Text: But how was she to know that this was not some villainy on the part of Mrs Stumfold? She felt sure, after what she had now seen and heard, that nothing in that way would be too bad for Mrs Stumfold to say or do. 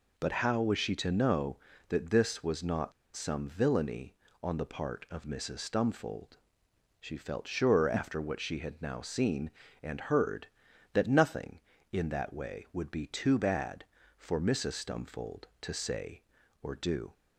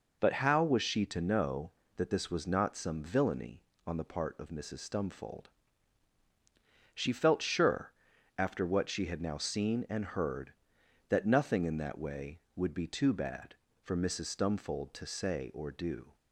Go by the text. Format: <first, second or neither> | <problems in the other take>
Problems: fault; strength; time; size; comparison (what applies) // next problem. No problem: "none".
second | pauses between "not" and "some"; slight; at 2.9 s; 0.23 s long